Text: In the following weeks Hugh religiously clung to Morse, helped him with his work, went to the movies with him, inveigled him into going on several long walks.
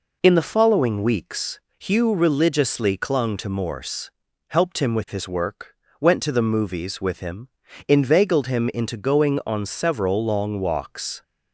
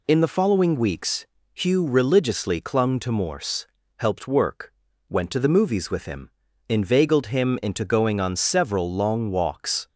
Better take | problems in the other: first | pauses between "weeks" and "Hugh"; slight; at 1.2 s; 0.30 s long; slight in the first // skips "him with his"; at 4.2 s

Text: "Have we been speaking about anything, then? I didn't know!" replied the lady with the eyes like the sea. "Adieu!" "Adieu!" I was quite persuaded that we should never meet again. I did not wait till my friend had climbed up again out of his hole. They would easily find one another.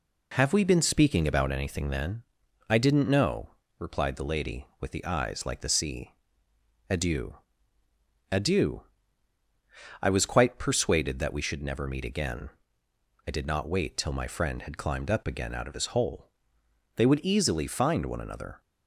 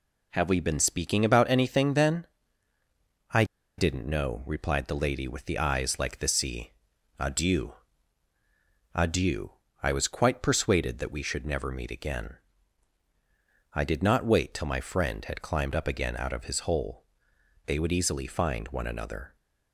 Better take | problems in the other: first | pauses between "I" and "didn't"; slight; at 3.4 s; 0.33 s long

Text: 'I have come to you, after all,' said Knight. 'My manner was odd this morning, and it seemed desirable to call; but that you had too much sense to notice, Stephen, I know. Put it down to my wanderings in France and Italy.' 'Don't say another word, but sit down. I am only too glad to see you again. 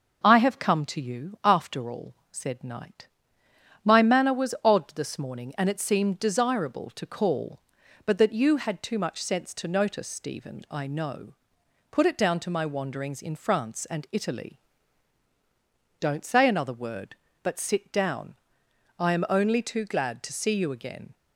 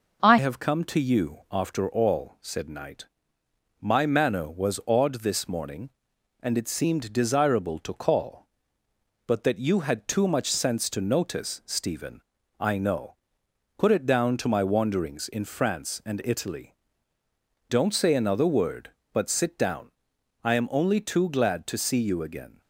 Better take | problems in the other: first | changes voice at "have"; from 0.3 s on; 22.3 s long

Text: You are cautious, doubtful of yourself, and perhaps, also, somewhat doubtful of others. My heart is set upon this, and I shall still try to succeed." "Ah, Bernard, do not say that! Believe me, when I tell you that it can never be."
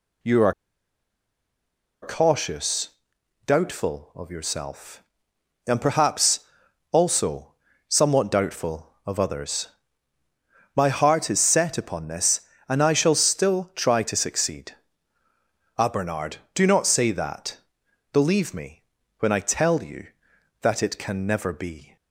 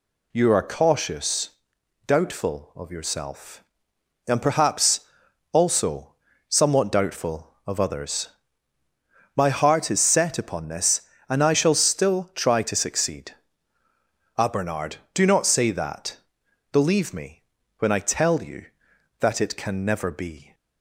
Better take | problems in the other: second | pauses between "are" and "cautious"; strong; at 0.5 s; 1.4 s long

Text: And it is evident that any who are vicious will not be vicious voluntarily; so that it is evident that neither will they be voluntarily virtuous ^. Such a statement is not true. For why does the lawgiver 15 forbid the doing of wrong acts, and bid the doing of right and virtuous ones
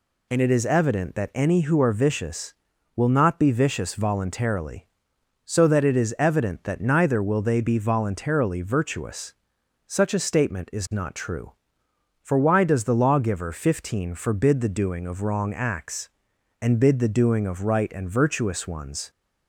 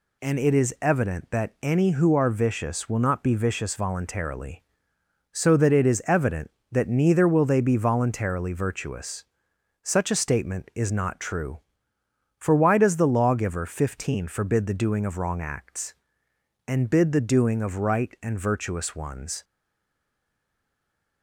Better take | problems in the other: first | stays silent after the last word; noticeable; from 19.4 s on; 1.8 s long

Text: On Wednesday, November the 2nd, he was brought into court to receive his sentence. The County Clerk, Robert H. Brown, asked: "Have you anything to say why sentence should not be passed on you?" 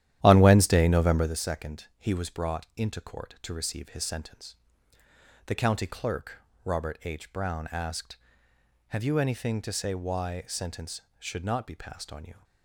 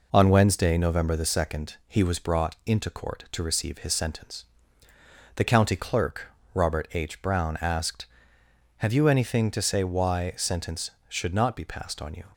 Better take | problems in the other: second | starts louder than the rest; strong; until 1.3 s; 12 dB

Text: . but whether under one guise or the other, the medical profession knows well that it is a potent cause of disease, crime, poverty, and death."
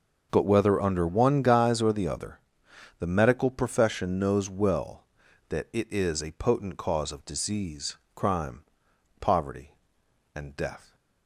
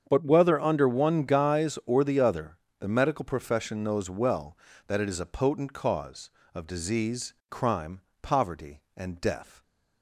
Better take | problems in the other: neither | starts louder than the rest; the same in both

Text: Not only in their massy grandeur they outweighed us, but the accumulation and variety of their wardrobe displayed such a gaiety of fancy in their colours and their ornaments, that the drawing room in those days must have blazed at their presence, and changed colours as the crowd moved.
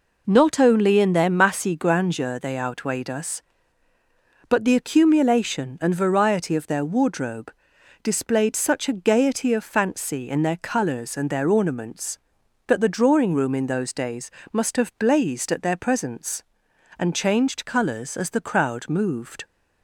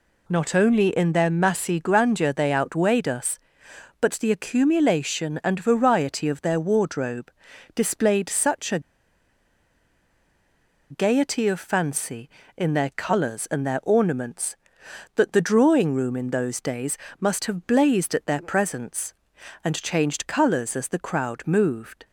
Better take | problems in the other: first | pauses between "wardrobe" and "displayed"; at 7.3 s; 0.44 s long; noticeable in the first // pauses between "a" and "gaiety"; strong; at 8.8 s; 2.1 s long // pauses between "days" and "must"; slight; at 16.9 s; 0.22 s long; slight in the first

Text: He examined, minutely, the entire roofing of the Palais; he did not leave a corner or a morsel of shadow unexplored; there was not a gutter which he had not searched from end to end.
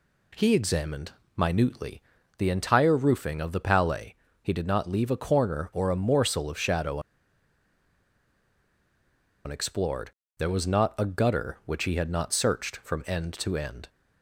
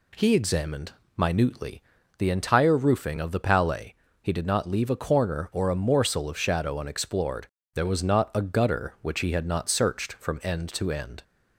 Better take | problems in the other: second | pauses between "shadow" and "unexplored"; strong; at 6.9 s; 2.4 s long

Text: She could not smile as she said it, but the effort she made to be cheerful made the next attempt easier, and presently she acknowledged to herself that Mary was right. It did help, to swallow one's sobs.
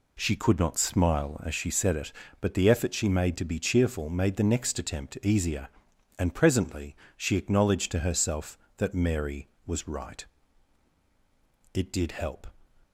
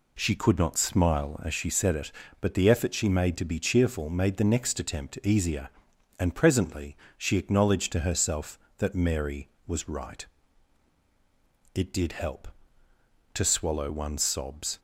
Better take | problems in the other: second | pauses between "presently" and "she"; slight; at 6.9 s; 0.22 s long; slight in the second // stops before "to swallow one's sobs"; at 12.8 s

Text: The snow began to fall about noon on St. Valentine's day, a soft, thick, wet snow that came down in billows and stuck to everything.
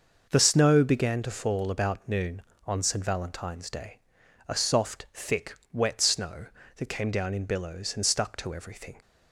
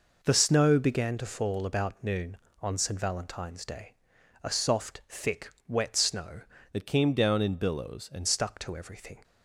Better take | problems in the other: first | changes voice from "that" to "and"; from 6.7 to 8.2 s; 1.5 s long

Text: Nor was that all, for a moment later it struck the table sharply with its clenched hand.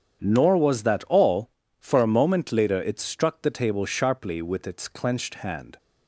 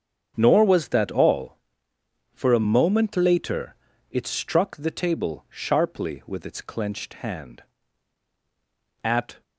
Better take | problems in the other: first | starts louder than the rest; strong; until 1.3 s; 7.5 dB; strong in the first // pauses between "later" and "it"; slight; at 3.7 s; 0.34 s long // goes on to say "At"; slight; from 9.0 s on; 0.38 s long

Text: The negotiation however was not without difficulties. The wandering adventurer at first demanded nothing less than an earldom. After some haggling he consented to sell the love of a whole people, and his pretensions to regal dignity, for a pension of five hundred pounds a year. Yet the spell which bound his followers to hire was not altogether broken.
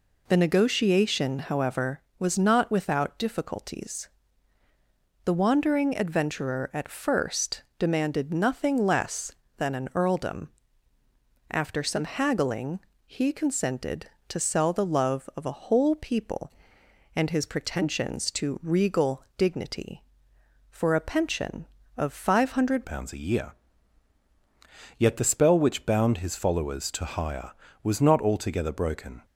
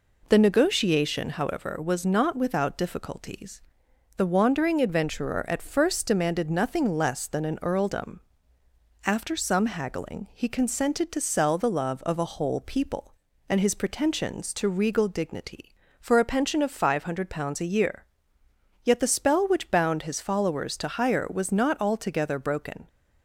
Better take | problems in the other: second | pauses between "first" and "demanded"; slight; at 7.6 s; 0.16 s long // pauses between "haggling" and "he"; slight; at 12.8 s; 0.24 s long // changes voice at "pounds"; from 22.8 s on; 6.4 s long

